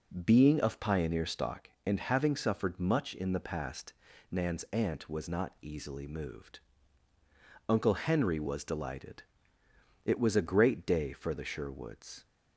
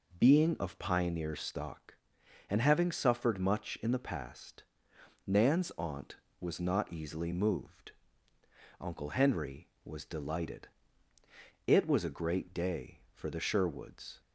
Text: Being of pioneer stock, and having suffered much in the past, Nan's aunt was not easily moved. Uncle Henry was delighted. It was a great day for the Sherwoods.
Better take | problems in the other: neither | none

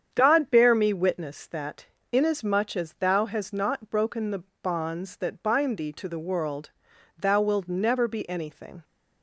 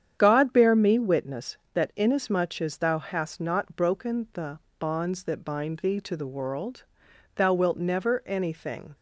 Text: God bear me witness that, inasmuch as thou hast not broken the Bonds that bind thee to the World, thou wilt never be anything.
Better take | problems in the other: first | starts louder than the rest; strong; until 1.2 s; 9 dB; strong in the first // pauses between "the" and "Bonds"; slight; at 4.5 s; 0.18 s long; slight in the first // skips "be"; at 8.2 s

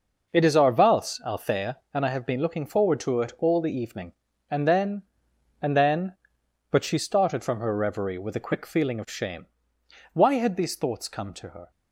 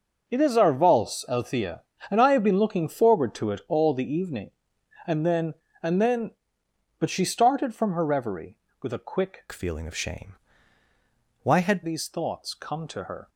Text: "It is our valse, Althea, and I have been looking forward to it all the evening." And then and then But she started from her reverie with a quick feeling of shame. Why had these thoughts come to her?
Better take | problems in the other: first | changes voice from "feeling" to "had"; from 9.5 to 11.8 s; 2.3 s long

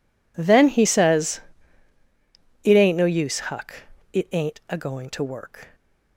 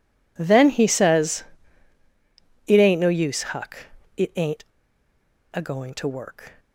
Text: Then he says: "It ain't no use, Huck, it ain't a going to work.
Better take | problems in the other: first | pauses between "ain't" and "a"; noticeable; at 4.6 s; 0.88 s long

